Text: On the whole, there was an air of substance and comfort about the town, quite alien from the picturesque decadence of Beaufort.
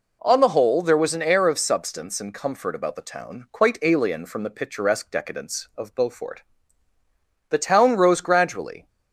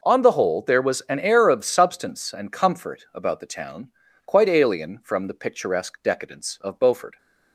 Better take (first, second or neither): second